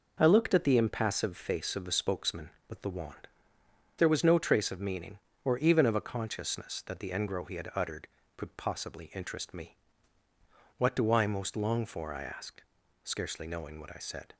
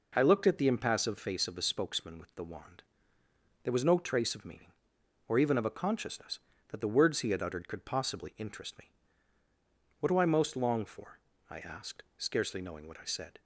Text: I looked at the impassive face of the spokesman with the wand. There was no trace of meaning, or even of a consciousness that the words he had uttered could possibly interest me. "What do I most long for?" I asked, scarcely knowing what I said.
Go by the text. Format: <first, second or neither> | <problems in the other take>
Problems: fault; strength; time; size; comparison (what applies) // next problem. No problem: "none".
second | says "engro" for "words"; at 7.1 s